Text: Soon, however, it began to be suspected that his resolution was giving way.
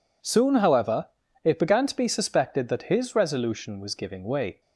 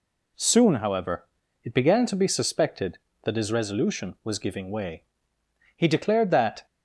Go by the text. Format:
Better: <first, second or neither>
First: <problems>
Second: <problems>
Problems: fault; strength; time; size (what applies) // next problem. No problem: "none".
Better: first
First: none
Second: goes on to say "He declared that"; noticeable; from 5.7 s on; 0.88 s long